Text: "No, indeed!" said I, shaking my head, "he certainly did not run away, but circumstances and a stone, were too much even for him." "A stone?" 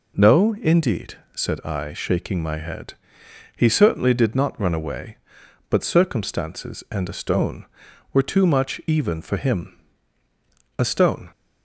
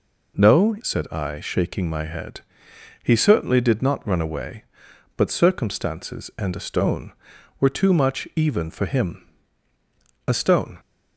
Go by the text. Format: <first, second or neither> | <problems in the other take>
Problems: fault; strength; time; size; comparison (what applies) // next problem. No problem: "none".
first | skips "indeed"; at 0.7 s